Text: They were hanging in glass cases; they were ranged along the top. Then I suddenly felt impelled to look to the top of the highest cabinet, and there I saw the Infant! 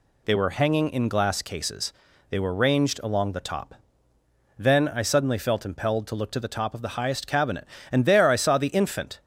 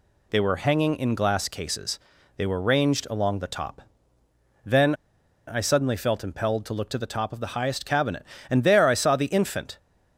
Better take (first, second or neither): first